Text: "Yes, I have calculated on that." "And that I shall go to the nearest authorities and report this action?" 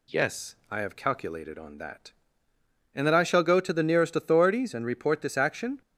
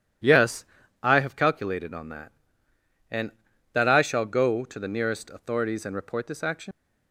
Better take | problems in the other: first | leaves "action" unfinished; at 6.7 s; 130 ms

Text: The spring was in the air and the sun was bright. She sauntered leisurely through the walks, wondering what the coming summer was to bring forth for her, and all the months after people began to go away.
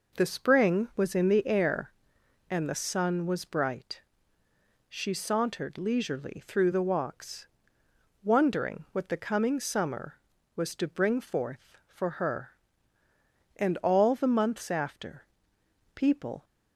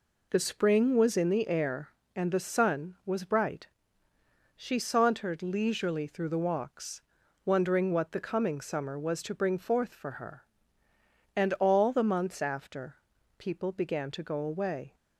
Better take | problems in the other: second | pauses between "after" and "people"; noticeable; at 15.2 s; 0.72 s long; also in the second // stops before "began to go away"; at 16.4 s

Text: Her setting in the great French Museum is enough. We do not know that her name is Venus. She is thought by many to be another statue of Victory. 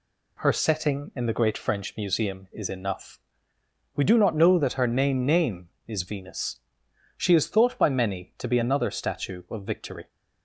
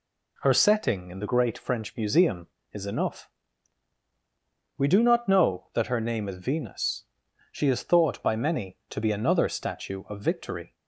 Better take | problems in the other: second | says "name" twice; at 5.2 s

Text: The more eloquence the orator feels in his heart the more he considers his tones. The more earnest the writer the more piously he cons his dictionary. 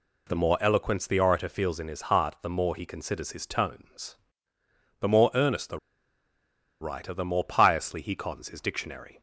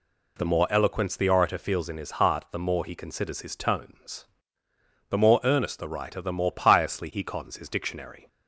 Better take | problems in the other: second | pauses between "the" and "writer"; at 5.7 s; 1.0 s long

